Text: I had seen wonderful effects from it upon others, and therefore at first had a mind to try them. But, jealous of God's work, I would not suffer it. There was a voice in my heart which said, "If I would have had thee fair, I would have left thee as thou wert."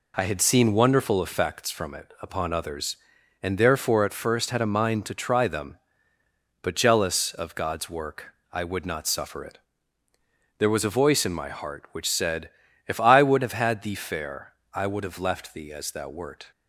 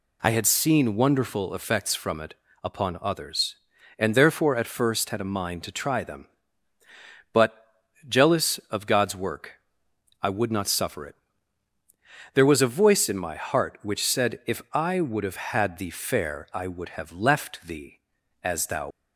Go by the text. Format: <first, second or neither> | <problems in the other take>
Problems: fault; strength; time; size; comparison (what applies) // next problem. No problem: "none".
first | pauses between "it" and "upon"; slight; at 2.3 s; 0.28 s long // stops before "wert"; at 18.9 s